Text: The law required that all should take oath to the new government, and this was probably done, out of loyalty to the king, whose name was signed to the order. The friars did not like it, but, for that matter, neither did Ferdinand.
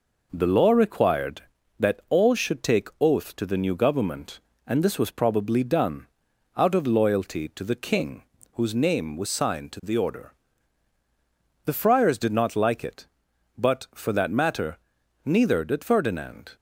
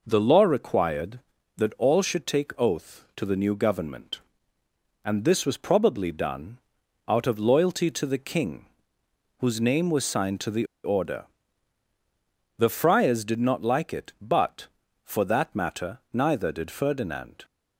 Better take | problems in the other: first | pauses between "the" and "order"; slight; at 10.6 s; 0.19 s long

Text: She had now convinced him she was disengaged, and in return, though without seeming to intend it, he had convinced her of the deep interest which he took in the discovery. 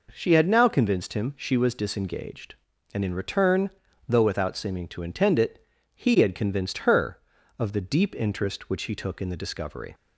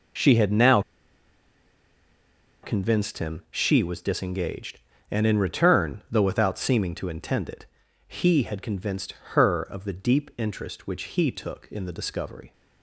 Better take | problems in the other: first | pauses between "now" and "convinced"; strong; at 0.8 s; 1.8 s long // pauses between "convinced" and "her"; slight; at 9.1 s; 0.18 s long

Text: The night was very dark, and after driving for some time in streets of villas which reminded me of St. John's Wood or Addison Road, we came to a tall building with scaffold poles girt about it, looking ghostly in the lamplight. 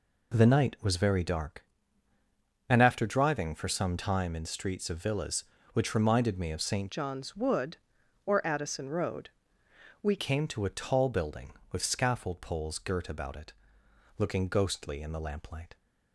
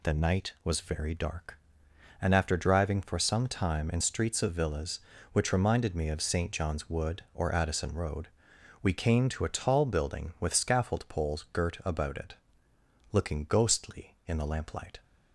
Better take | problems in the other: second | changes voice from "John's" to "we"; from 6.9 to 10.1 s; 3.2 s long

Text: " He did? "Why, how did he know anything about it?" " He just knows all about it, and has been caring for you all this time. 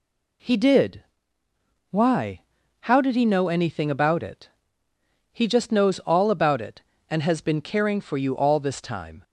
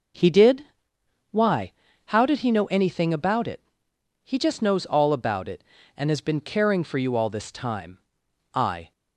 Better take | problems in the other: first | goes on to say "I"; slight; from 8.5 s on; 0.38 s long

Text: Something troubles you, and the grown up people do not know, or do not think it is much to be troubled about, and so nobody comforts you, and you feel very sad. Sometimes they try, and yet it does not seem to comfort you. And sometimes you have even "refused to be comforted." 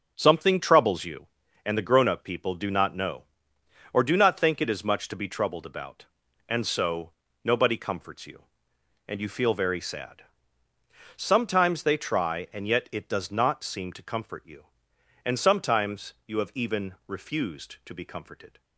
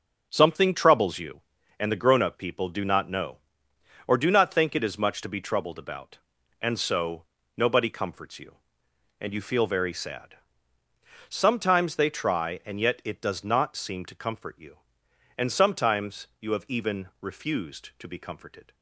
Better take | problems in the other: neither | starts louder than the rest; the same in both // pauses between "so" and "nobody"; slight; the same in both // pauses between "sometimes" and "you"; slight; the same in both

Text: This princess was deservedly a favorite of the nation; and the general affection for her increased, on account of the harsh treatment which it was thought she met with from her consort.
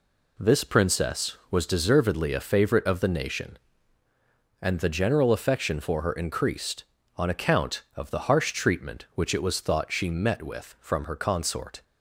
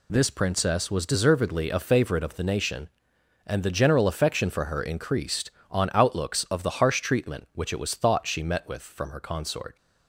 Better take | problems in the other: first | says "outlooks" for "account"; at 5.9 s

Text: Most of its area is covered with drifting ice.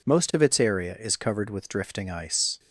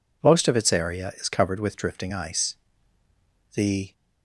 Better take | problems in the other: first | goes on to say "The"; slight; from 3.5 s on; 0.38 s long

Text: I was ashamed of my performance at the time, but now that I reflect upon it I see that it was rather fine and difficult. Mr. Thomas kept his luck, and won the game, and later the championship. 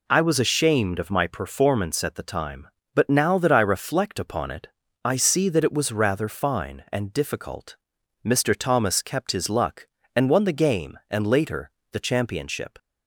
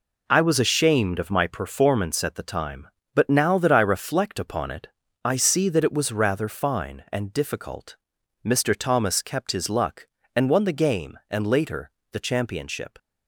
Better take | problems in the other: first | gets quieter; strong; throughout; 8 dB // pauses between "it" and "I"; slight; at 4.8 s; 0.36 s long; slight in the first // pauses between "later" and "the"; slight; at 11.8 s; 0.20 s long; slight in the first

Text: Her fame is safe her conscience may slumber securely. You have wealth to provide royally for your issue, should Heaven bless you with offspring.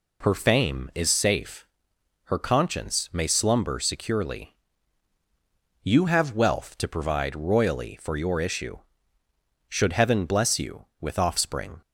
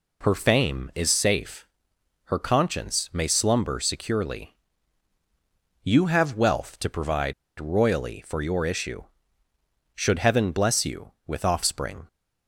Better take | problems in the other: first | pauses between "safe" and "her"; noticeable; at 1.6 s; 0.58 s long; noticeable in the first // pauses between "provide" and "royally"; slight; at 7.3 s; 0.25 s long

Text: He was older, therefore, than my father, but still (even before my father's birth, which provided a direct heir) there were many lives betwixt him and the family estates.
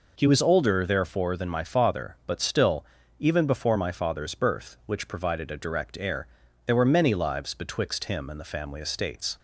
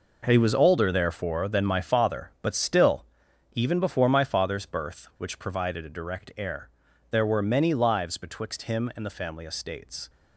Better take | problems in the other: first | gets quieter; strong; throughout; 11.5 dB

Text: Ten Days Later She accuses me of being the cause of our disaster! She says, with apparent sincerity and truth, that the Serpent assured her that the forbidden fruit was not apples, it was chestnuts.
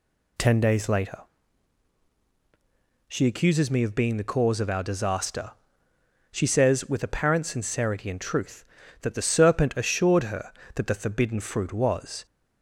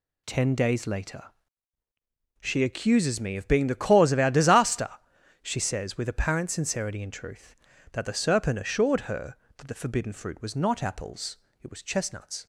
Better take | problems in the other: second | pauses between "Later" and "She"; strong; at 1.2 s; 1.8 s long; also in the second // stops before "not apples it was chestnuts"; at 12.2 s

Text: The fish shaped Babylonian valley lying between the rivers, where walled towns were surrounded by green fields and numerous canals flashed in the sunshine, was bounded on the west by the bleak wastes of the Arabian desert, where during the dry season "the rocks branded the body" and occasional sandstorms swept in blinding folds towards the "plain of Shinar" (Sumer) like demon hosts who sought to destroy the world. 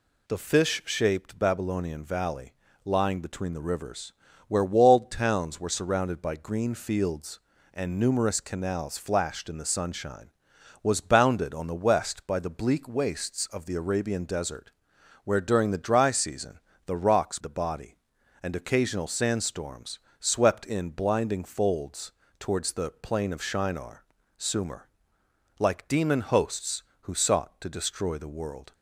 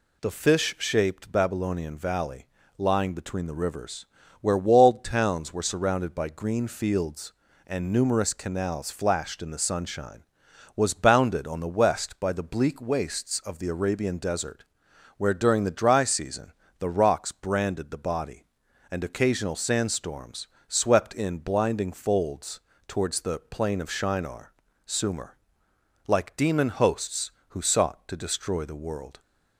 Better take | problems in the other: second | pauses between "valley" and "lying"; slight; at 2.5 s; 0.30 s long; slight in the second // pauses between "season" and "the"; slight; at 16.5 s; 0.28 s long; slight in the second // skips "branded"; at 17.3 s // pauses between "sandstorms" and "swept"; slight; at 20.0 s; 0.18 s long; slight in the second // pauses between "folds" and "towards"; slight; at 22.1 s; 0.30 s long; slight in the second

